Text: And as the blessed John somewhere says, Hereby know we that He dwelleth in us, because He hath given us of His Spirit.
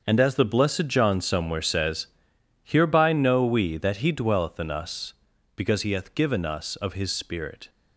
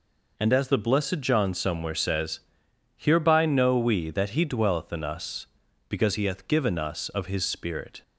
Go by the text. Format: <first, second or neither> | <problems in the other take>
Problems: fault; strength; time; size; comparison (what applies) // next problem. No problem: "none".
second | gets quieter; strong; throughout; 11.5 dB